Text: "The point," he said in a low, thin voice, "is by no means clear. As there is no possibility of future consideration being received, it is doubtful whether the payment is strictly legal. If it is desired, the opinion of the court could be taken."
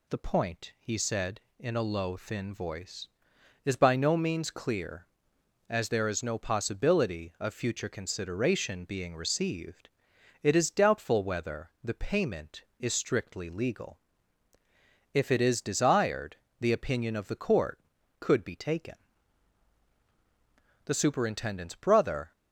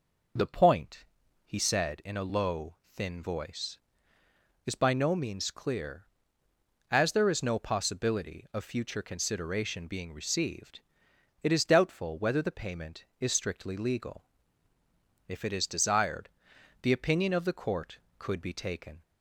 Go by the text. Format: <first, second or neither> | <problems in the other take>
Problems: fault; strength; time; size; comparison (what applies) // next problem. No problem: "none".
second | goes on to say "The superintendent's brother"; from 20.8 s on; 1.4 s long